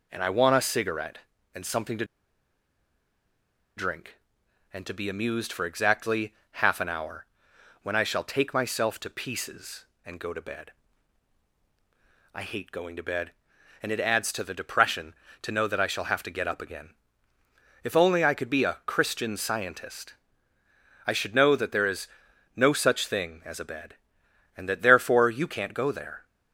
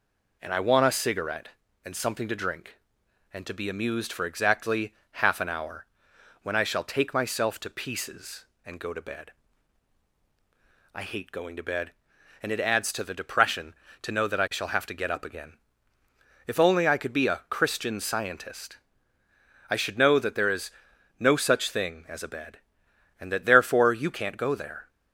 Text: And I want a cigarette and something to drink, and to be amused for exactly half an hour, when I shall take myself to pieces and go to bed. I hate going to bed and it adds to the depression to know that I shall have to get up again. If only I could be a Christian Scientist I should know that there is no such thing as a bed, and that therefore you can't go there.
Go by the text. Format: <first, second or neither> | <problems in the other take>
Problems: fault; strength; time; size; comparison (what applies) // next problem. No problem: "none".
second | pauses between "to" and "drink"; strong; at 2.0 s; 1.7 s long // pauses between "exactly" and "half"; slight; at 6.3 s; 0.18 s long; slight in the second // pauses between "Scientist" and "I"; noticeable; at 20.1 s; 0.92 s long; noticeable in the second // pauses between "is" and "no"; noticeable; at 22.0 s; 0.48 s long; noticeable in the second